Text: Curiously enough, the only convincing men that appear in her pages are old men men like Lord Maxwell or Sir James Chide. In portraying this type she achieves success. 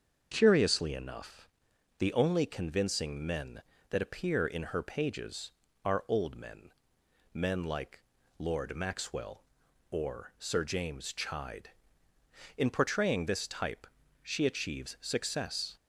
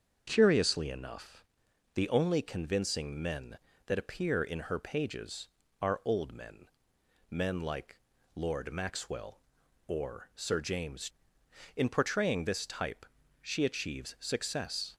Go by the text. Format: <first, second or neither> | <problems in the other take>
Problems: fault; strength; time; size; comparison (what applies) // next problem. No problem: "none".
first | starts louder than the rest; until 1.2 s; 7 dB; also in the first // pauses between "men" and "men"; noticeable; at 6.6 s; 0.64 s long; noticeable in the first // pauses between "like" and "Lord"; at 7.9 s; 0.38 s long; also in the first // skips "Chide"; at 11.4 s // pauses between "type" and "she"; at 13.0 s; 0.38 s long; also in the first